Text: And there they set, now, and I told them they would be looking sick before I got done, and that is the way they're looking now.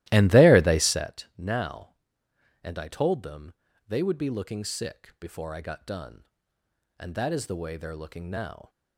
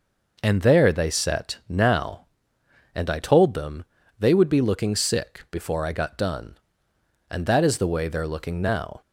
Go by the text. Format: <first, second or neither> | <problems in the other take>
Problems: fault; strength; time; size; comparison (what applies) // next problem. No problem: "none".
second | starts louder than the rest; strong; until 1.0 s; 16 dB // pauses between "them" and "they"; slight; at 3.5 s; 0.34 s long; slight in the second